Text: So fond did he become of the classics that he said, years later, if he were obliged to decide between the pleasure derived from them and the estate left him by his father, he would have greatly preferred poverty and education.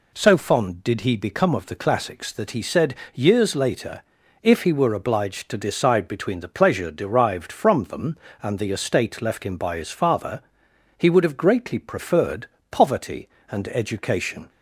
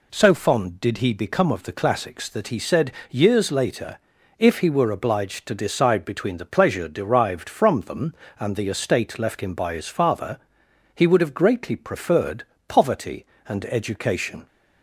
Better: neither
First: pauses between "preferred" and "poverty"; slight; at 12.4 s; 0.24 s long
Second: pauses between "preferred" and "poverty"; slight; at 12.4 s; 0.24 s long

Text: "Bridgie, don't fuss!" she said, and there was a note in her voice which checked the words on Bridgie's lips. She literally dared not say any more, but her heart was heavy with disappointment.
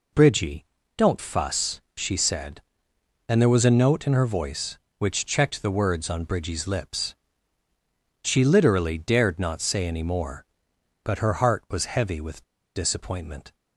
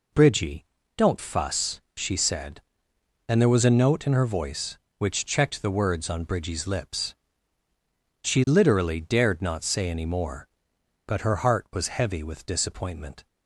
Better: second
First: pauses between "with" and "disappointment"; slight; at 12.4 s; 0.31 s long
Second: none

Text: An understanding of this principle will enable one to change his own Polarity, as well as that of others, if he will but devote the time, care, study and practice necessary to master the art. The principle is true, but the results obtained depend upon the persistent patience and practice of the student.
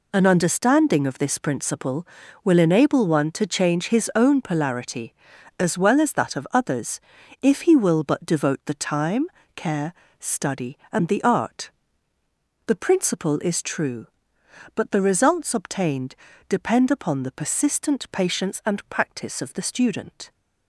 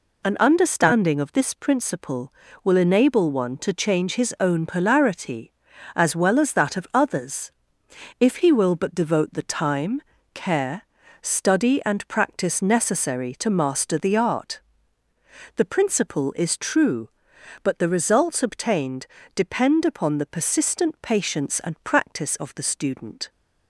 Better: second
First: skips "practice necessary to master"; at 11.0 s // pauses between "obtained" and "depend"; slight; at 16.1 s; 0.34 s long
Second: pauses between "obtained" and "depend"; slight; at 19.0 s; 0.30 s long

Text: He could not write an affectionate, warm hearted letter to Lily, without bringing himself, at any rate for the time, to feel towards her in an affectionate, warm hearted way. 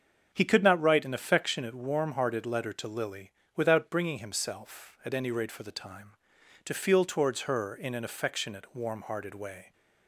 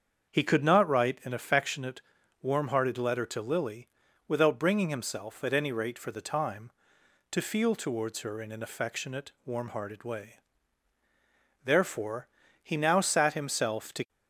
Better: first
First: starts louder than the rest; strong; until 1.3 s; 7 dB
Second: starts louder than the rest; strong; until 1.3 s; 7 dB // goes on to say "Therefore he now sat himself to"; strong; from 11.6 s on; 2.4 s long

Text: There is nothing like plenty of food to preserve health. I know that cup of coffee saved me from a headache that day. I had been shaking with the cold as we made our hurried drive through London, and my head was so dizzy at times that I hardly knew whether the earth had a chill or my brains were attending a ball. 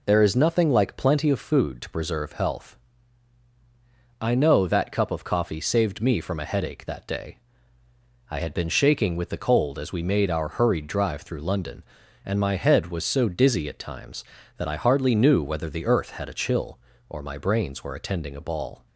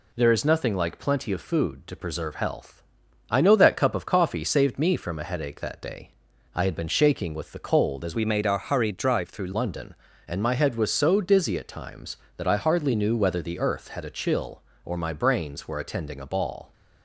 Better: first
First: none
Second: changes voice from "we" to "through"; from 8.1 to 9.5 s; 1.4 s long

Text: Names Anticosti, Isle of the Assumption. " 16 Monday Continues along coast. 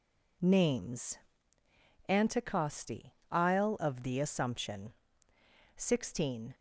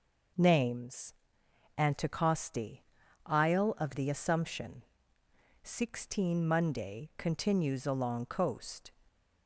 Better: second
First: pauses between "Names" and "Anticosti"; noticeable; at 1.1 s; 0.92 s long // stops before "Monday Continues along coast"; at 6.5 s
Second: pauses between "Names" and "Anticosti"; noticeable; at 1.1 s; 0.64 s long

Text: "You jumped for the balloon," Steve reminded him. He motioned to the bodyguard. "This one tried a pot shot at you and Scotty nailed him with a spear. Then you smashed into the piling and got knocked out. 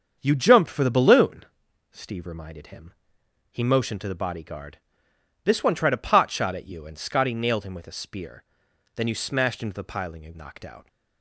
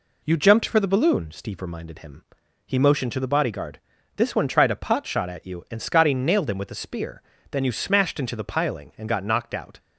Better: second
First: starts louder than the rest; strong; until 1.2 s; 7 dB // skips "got"; at 10.3 s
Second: none

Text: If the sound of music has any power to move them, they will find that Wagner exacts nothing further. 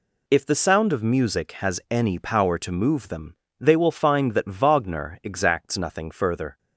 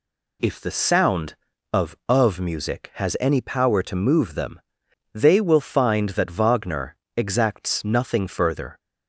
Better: first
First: none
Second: says "of" twice; at 2.0 s // pauses between "Wagner" and "exacts"; slight; at 6.9 s; 0.18 s long

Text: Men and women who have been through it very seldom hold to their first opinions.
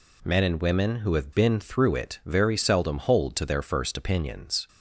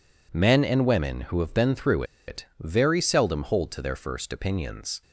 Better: first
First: none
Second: pauses between "through" and "it"; slight; at 2.0 s; 0.24 s long

